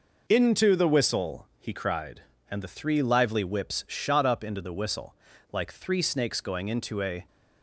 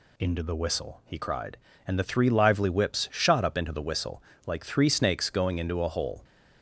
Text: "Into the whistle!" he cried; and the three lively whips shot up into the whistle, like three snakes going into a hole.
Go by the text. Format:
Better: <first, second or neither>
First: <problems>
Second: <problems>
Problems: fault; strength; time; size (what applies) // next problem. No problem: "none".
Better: second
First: stops before "hole"; at 7.2 s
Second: none